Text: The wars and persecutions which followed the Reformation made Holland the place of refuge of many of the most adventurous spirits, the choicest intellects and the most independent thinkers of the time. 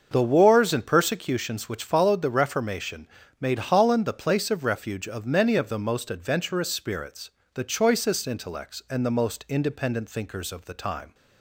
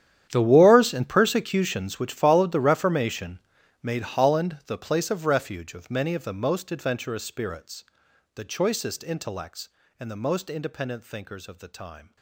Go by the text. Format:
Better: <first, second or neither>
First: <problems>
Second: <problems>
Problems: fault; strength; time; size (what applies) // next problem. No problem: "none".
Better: first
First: starts louder than the rest; until 1.1 s; 6.5 dB // pauses between "Reformation" and "made"; slight; at 3.0 s; 0.32 s long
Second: gets quieter; strong; throughout; 18.5 dB // starts louder than the rest; strong; until 1.3 s; 10.5 dB // pauses between "Reformation" and "made"; noticeable; at 3.3 s; 0.46 s long